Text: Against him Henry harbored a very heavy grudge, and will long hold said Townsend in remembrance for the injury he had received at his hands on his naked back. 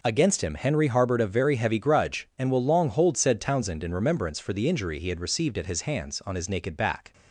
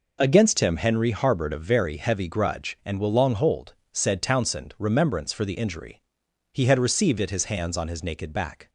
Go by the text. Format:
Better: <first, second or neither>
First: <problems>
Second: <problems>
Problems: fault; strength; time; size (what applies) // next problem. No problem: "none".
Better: first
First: none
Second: pauses between "hold" and "said"; slight; at 3.7 s; 0.20 s long // skips "in"; at 4.7 s // pauses between "injury" and "he"; noticeable; at 6.0 s; 0.50 s long